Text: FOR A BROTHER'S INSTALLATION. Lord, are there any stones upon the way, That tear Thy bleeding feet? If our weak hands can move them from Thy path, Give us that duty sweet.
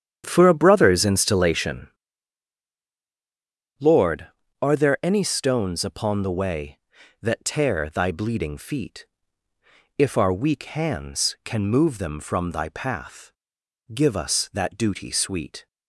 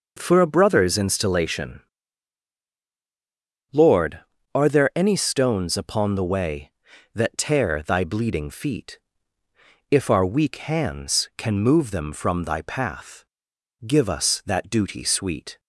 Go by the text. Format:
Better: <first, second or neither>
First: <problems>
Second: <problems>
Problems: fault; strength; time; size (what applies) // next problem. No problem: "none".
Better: second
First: starts louder than the rest; strong; until 2.0 s; 9 dB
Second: none